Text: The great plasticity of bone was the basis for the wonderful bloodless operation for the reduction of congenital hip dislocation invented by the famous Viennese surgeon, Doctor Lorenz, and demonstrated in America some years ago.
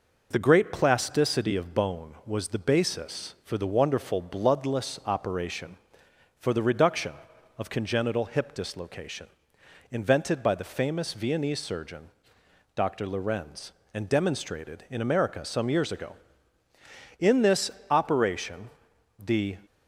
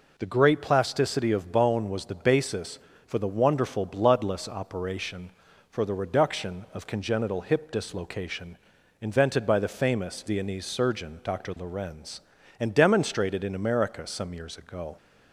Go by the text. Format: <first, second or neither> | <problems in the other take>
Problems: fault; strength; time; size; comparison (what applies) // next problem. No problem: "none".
second | pauses between "dislocation" and "invented"; noticeable; at 9.2 s; 0.63 s long; also in the second // goes on to say "In this operation the"; strong; from 17.1 s on; 2.4 s long